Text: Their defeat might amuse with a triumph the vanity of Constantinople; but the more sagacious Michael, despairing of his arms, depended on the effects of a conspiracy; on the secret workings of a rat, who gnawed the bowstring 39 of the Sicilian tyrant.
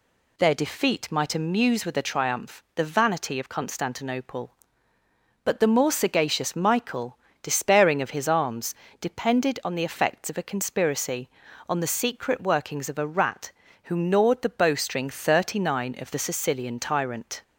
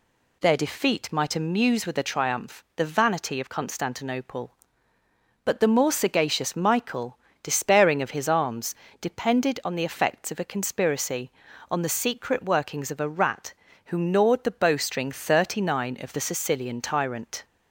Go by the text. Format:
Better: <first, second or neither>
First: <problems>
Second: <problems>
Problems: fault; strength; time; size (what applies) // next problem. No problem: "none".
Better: neither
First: none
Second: none